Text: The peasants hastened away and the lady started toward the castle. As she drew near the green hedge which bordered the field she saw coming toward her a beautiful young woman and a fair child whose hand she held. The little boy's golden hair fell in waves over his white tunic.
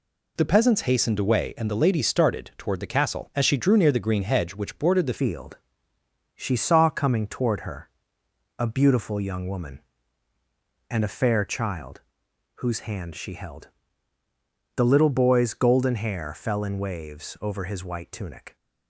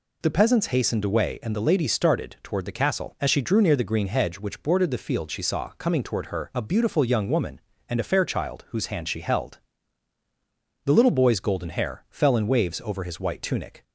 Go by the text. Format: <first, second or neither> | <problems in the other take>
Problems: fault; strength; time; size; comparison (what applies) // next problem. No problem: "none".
second | changes voice at "field"; from 5.1 s on; 13.4 s long // pauses between "field" and "she"; noticeable; at 5.5 s; 0.78 s long // pauses between "her" and "a"; noticeable; at 7.8 s; 0.70 s long // pauses between "child" and "whose"; noticeable; at 12.0 s; 0.56 s long